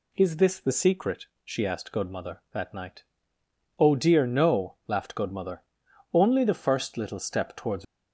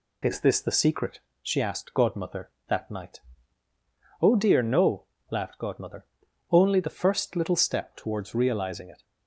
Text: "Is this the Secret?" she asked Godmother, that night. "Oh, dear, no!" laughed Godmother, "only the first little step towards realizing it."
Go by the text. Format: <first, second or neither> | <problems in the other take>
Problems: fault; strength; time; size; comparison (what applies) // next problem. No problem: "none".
second | stops before "realizing it"; at 7.8 s